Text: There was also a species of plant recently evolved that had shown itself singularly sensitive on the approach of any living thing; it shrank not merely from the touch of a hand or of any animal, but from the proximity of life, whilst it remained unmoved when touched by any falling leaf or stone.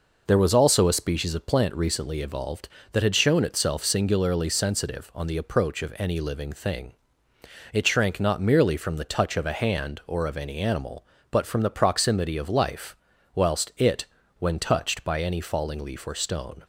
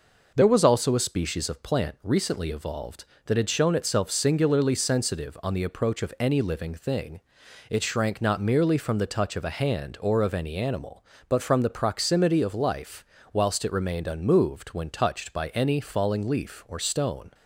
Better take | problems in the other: second | skips "remained unmoved"; at 14.2 s

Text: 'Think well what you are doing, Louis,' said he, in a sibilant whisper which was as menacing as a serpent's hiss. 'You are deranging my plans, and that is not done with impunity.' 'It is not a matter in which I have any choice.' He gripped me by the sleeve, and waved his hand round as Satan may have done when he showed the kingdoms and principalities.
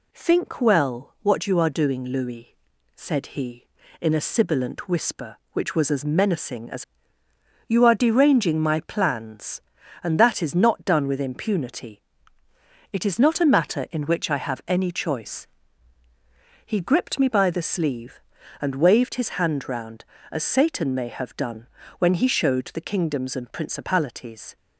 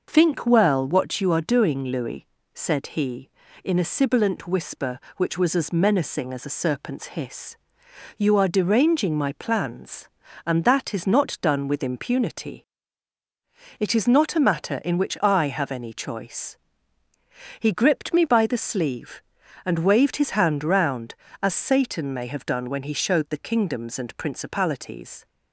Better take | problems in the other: second | skips "a serpent's hiss"; at 7.2 s // pauses between "done" and "when"; slight; at 21.6 s; 0.32 s long

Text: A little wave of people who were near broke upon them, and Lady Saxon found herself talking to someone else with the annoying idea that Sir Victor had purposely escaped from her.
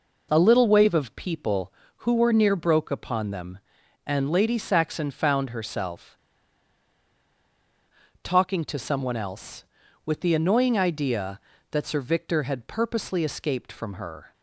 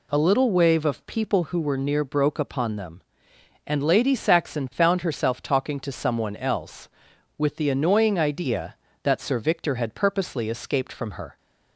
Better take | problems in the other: second | pauses between "herself" and "talking"; strong; at 6.1 s; 2.0 s long

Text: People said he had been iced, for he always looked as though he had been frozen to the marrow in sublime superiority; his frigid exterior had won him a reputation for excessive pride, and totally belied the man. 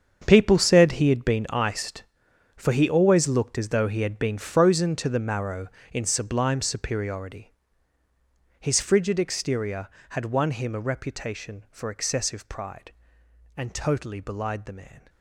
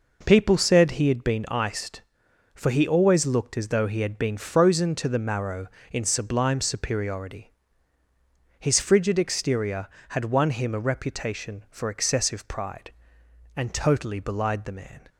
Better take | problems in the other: second | gets quieter; strong; throughout; 14 dB

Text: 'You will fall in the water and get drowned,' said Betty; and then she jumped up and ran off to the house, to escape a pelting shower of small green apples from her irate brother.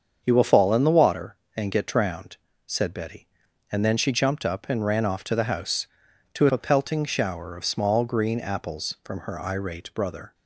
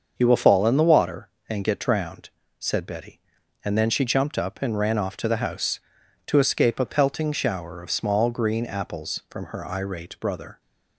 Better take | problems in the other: second | starts louder than the rest; until 1.2 s; 7 dB; also in the second // skips "escape"; at 6.4 s

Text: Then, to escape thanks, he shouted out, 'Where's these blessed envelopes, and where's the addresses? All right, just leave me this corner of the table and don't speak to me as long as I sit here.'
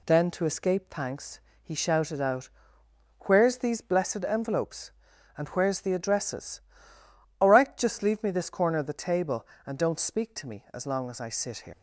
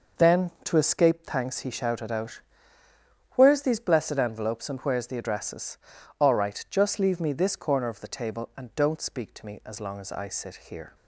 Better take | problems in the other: second | leaves "here" unfinished; at 11.7 s; 115 ms

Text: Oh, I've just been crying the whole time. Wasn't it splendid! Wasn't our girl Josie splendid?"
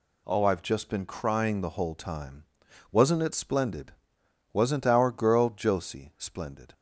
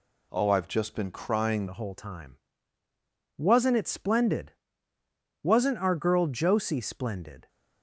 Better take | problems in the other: first | changes voice at "the"; from 1.6 s on; 5.8 s long

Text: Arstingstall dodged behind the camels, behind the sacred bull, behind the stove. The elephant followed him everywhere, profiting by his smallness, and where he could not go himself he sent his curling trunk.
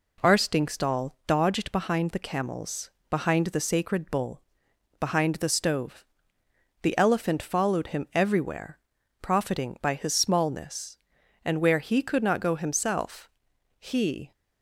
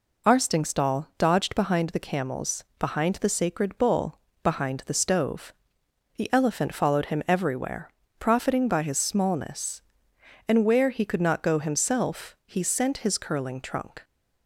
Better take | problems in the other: second | pauses between "himself" and "he"; noticeable; at 13.2 s; 0.50 s long // stops before "sent his curling trunk"; at 14.3 s

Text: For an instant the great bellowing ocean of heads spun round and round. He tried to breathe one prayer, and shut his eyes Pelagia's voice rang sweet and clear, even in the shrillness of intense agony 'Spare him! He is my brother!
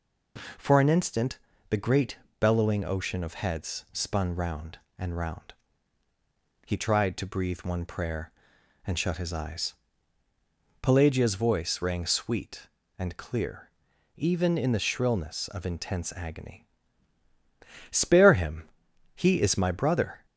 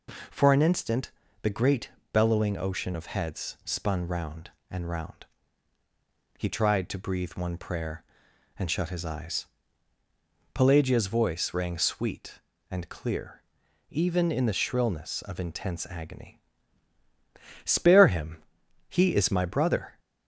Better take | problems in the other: neither | pauses between "instant" and "the"; slight; the same in both // pauses between "great" and "bellowing"; slight; the same in both // pauses between "eyes" and "Pelagia's"; the same in both // pauses between "agony" and "Spare"; the same in both

